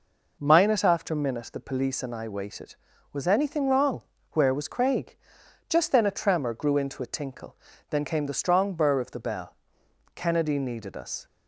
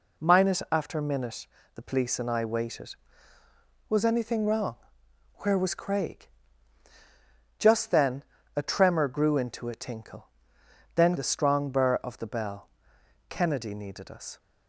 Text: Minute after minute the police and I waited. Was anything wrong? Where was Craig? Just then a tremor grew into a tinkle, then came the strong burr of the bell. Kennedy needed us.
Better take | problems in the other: first | pauses between "minute" and "the"; slight; at 1.4 s; 0.30 s long // pauses between "then" and "a"; slight; at 8.2 s; 0.32 s long // skips "came"; at 11.1 s

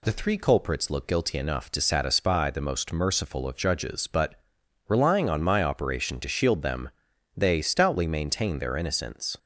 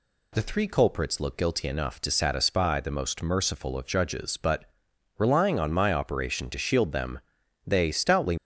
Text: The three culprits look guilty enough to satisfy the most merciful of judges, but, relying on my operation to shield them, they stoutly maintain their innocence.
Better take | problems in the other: first | stops before "maintain their innocence"; at 8.3 s

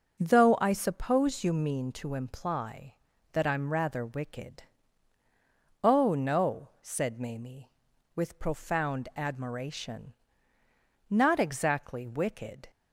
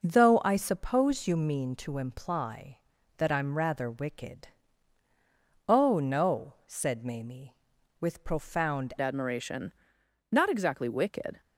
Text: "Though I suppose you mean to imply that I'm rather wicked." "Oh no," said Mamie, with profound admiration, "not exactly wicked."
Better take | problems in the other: first | changes voice at "admiration"; from 9.0 s on; 2.4 s long

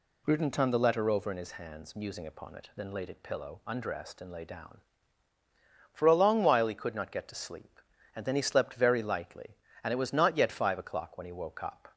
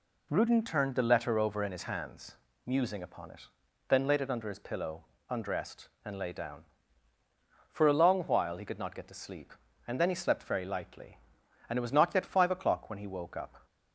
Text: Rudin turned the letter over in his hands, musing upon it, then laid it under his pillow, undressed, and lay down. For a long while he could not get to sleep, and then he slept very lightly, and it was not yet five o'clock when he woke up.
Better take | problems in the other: second | skips "under his"; at 3.2 s

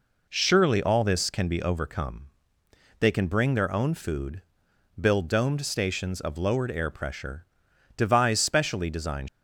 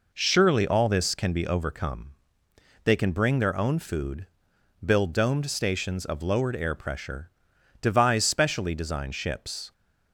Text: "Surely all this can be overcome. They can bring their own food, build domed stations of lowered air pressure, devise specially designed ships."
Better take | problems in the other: second | stops before "ships"; at 9.2 s

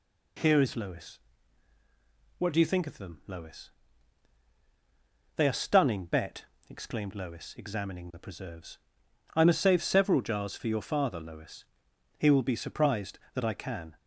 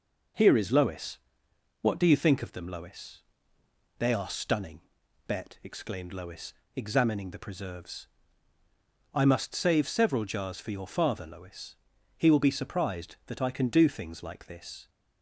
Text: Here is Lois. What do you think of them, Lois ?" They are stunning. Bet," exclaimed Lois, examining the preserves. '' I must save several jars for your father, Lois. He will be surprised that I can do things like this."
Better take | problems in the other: second | stops before "do things like this"; at 13.9 s

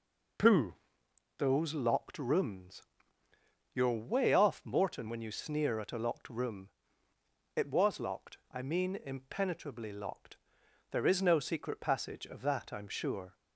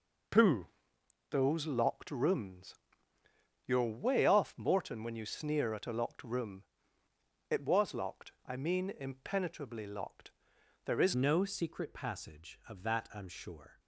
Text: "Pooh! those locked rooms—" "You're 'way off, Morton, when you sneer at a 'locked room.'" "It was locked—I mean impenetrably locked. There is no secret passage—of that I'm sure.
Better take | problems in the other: first | changes voice at "no"; from 11.1 s on; 2.6 s long

